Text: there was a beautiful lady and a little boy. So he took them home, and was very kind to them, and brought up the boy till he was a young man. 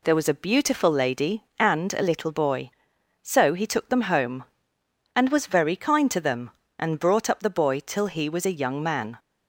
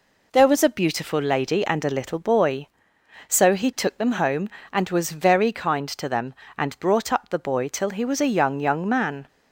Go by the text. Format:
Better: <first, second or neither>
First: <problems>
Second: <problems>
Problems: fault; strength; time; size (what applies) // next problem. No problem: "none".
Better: first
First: none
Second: says "young" twice; at 8.5 s